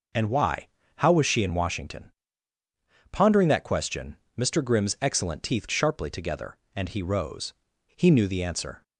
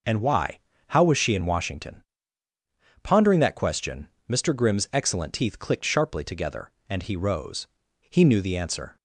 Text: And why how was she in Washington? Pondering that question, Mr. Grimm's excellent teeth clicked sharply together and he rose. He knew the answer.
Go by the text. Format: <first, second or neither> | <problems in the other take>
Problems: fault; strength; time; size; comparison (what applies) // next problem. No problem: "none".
second | pauses between "why" and "how"; slight; at 0.6 s; 0.30 s long; slight in the second // skips "clicked"; at 5.6 s